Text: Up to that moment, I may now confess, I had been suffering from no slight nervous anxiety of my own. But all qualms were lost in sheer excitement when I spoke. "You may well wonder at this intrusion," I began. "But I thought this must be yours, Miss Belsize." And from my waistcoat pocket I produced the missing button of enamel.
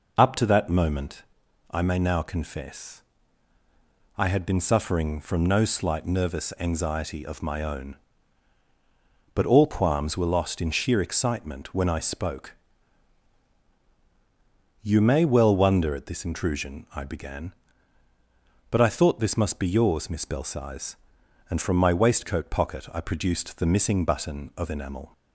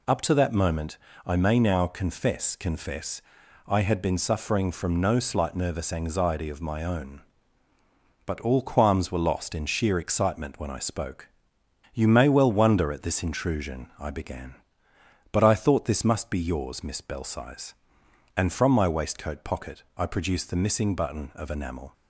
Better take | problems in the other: first | says "confess" twice; at 2.5 s

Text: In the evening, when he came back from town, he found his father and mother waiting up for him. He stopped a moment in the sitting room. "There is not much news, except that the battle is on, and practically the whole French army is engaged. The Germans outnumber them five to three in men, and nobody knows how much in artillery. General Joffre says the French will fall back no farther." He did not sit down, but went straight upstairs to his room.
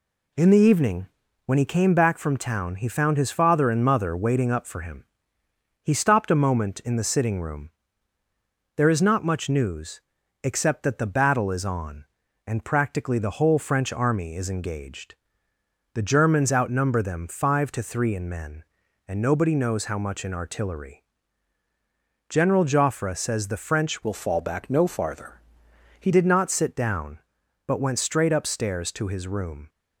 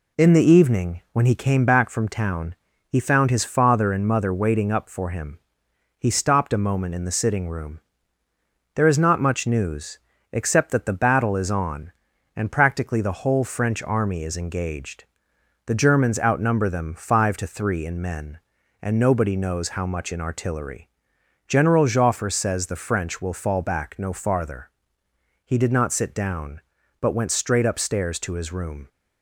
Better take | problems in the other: second | changes voice from "will" to "He"; from 24.0 to 26.1 s; 2.1 s long

